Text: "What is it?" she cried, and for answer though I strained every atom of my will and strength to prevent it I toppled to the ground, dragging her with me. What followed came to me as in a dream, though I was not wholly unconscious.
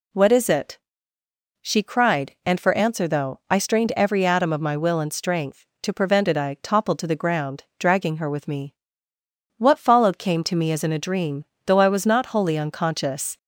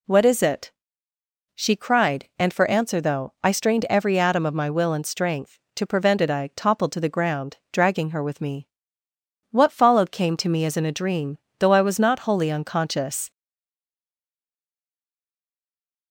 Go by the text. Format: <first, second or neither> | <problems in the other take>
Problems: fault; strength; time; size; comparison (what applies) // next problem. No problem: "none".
first | stays silent after the last word; strong; from 13.3 s on; 2.8 s long